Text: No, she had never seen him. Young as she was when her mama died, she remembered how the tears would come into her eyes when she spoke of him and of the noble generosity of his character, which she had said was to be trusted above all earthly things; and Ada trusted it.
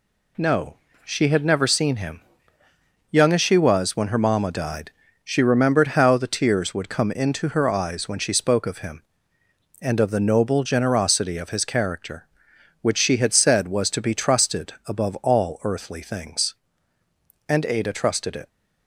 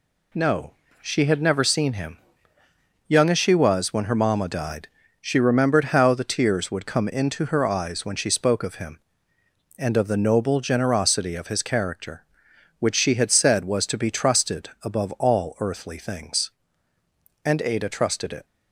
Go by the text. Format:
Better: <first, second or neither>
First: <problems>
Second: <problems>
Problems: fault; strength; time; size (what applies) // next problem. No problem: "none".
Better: neither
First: none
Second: none